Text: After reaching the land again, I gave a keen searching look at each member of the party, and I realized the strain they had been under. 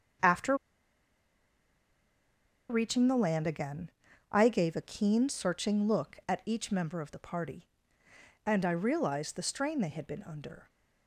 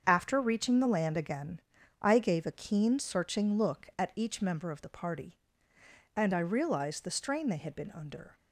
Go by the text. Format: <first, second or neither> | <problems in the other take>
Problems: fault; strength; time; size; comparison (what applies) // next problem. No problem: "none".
second | starts louder than the rest; strong; until 3.3 s; 7.5 dB; strong in the second // pauses between "After" and "reaching"; strong; at 0.5 s; 2.1 s long